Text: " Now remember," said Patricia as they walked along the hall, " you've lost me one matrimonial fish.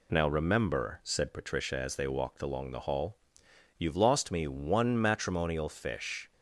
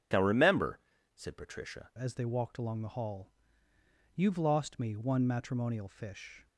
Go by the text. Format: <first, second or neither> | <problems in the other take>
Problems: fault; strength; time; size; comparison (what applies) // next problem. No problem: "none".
first | starts louder than the rest; strong; until 1.4 s; 8.5 dB // changes voice at "as"; from 1.9 s on; 4.5 s long